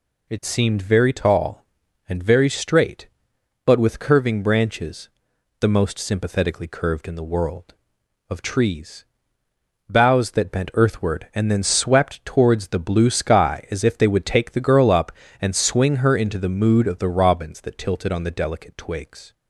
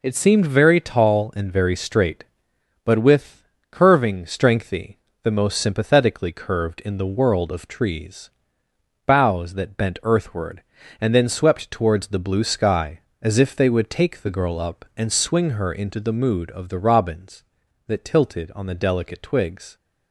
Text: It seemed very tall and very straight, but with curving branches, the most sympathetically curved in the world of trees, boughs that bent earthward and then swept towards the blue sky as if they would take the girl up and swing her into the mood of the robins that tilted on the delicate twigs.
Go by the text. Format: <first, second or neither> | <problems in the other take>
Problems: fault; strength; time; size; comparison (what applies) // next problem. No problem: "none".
first | pauses between "with" and "curving"; slight; at 3.4 s; 0.24 s long // says "strengthy" for "branches"; at 4.2 s